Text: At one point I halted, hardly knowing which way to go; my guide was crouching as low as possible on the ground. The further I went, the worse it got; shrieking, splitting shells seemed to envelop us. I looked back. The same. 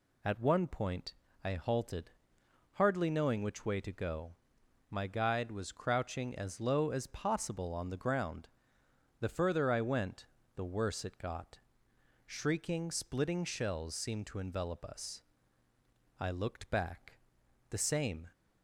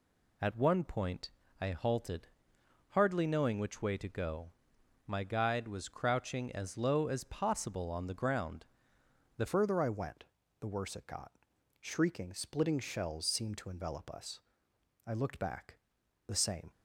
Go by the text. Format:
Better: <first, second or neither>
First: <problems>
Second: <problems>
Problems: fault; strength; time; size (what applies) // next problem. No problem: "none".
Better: first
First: pauses between "point" and "I"; slight; at 1.1 s; 0.30 s long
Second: pauses between "point" and "I"; slight; at 1.3 s; 0.30 s long // changes voice at "further"; from 9.4 s on; 7.3 s long